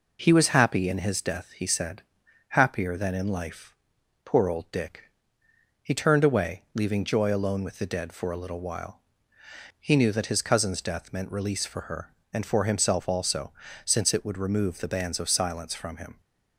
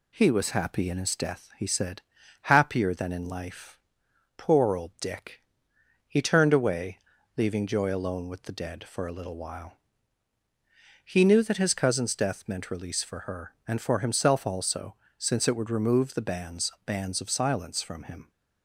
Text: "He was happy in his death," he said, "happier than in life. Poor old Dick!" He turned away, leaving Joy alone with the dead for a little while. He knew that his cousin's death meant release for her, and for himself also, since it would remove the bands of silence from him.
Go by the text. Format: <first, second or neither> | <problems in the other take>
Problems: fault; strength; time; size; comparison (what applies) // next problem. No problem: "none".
first | says "bands" twice; at 16.8 s